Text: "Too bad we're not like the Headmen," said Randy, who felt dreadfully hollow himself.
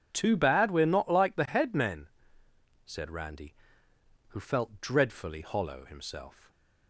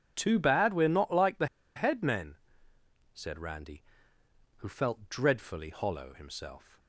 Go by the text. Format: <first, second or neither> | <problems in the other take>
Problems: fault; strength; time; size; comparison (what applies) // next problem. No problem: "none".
first | pauses between "the" and "Headmen"; slight; at 1.4 s; 0.30 s long